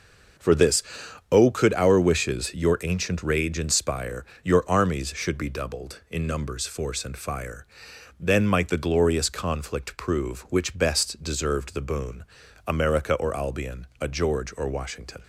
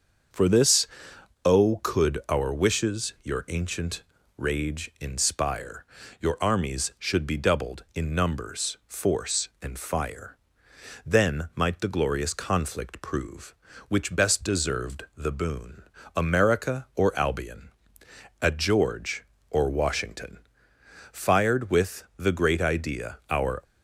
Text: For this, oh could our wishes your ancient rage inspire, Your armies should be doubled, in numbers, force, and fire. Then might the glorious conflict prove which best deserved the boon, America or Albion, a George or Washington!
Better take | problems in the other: first | starts louder than the rest; until 1.9 s; 7 dB; also in the first // pauses between "ancient" and "rage"; slight; at 4.0 s; 0.36 s long // goes on to say "Fired with the great idea our"; strong; from 21.1 s on; 2.5 s long

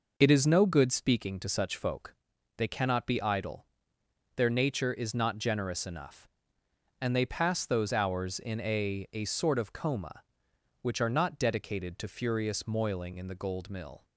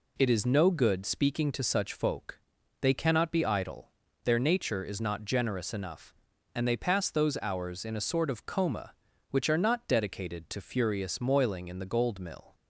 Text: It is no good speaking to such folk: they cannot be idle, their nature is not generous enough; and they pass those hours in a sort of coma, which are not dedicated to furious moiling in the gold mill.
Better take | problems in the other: second | says "a" twice; at 9.1 s

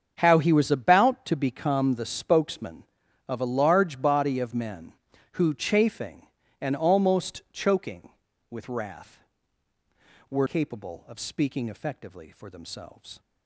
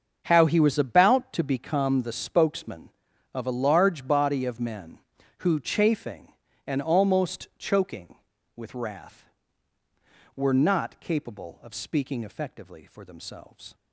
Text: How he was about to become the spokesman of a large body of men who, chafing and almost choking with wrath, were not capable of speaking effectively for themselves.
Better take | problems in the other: second | starts louder than the rest; strong; until 1.1 s; 7 dB; also in the second // skips "not"; at 10.4 s

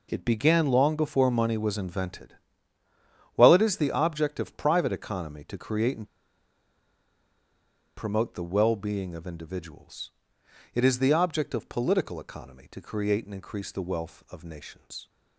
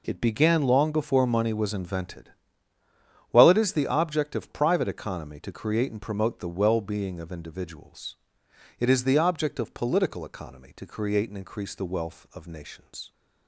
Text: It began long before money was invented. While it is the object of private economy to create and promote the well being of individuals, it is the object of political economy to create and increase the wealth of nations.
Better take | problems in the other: second | pauses between "and" and "promote"; strong; at 6.0 s; 1.8 s long

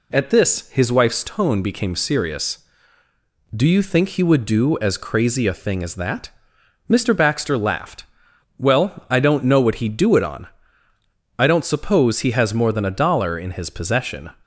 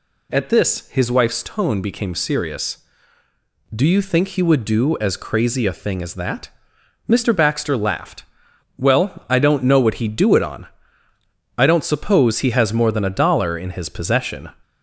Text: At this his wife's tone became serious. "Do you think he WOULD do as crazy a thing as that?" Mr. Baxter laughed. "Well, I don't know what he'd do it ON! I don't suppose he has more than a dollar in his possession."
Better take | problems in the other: first | gets louder; slight; throughout; 2.5 dB

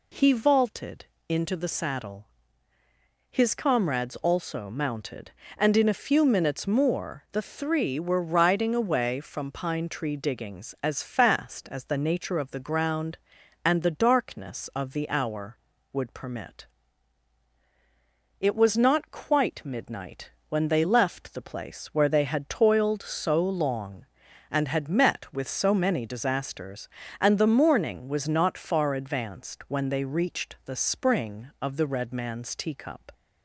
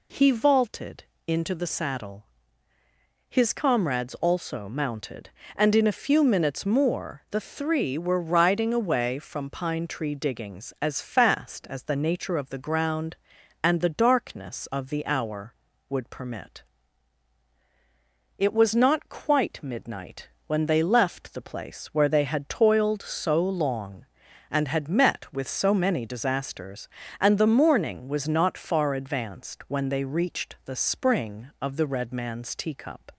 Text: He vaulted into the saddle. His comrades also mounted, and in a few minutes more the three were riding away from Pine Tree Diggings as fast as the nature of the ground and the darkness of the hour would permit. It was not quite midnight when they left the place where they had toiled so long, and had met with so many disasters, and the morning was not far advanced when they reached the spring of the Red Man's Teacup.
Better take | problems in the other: neither | pauses between "vaulted" and "into"; slight; the same in both // pauses between "midnight" and "when"; slight; the same in both

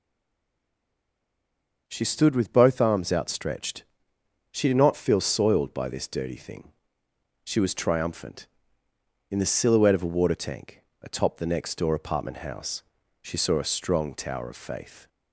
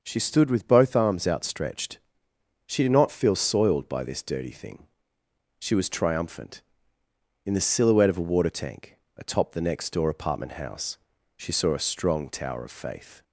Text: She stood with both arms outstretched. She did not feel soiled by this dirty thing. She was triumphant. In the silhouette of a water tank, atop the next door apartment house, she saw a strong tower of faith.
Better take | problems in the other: second | stays silent before the first word; noticeable; until 1.8 s; 1.8 s long

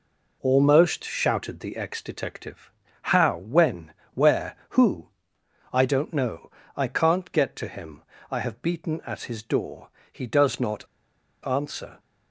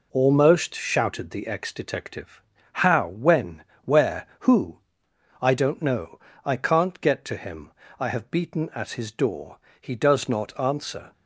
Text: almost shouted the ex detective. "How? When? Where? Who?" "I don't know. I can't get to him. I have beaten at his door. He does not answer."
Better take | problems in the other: second | pauses between "not" and "answer"; noticeable; at 10.8 s; 0.58 s long

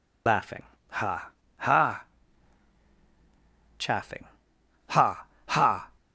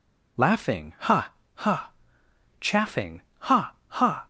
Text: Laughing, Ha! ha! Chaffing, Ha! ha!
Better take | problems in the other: second | loses the start of "Laughing"; at 0.2 s; 90 ms

